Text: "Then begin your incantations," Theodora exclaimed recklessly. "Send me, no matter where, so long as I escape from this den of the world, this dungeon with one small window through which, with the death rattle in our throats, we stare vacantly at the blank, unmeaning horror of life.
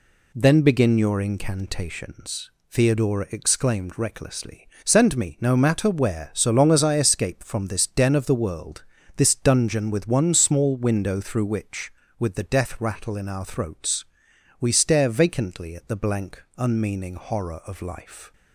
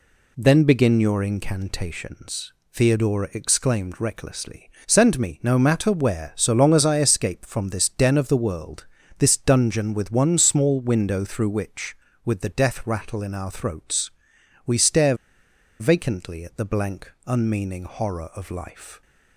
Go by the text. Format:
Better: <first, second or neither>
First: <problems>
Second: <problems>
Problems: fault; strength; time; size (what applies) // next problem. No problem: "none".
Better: first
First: none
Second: pauses between "stare" and "vacantly"; noticeable; at 15.1 s; 0.65 s long